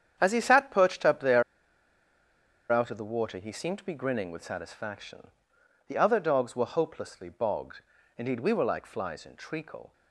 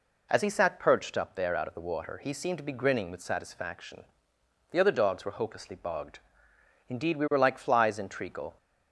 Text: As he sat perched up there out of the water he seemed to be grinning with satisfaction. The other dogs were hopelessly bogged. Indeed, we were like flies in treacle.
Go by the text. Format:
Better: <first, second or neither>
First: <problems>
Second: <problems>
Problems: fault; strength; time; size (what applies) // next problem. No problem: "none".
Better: second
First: starts louder than the rest; strong; until 1.2 s; 8.5 dB // pauses between "there" and "out"; strong; at 1.4 s; 1.2 s long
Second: none